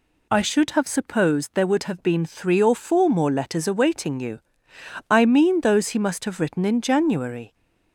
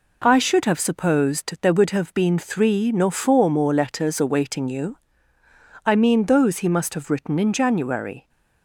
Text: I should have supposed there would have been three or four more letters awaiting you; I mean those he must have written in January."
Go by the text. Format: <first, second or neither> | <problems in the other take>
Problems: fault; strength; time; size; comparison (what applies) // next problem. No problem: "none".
first | says "nor" for "or"; at 2.9 s